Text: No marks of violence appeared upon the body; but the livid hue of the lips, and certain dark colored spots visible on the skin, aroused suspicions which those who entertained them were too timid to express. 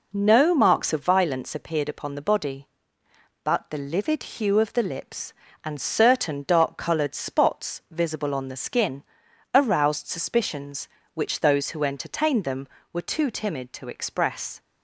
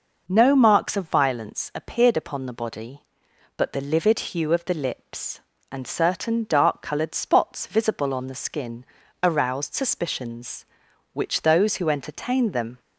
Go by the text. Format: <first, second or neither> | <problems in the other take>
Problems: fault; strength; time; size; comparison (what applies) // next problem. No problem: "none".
first | stops before "were too timid to express"; at 12.7 s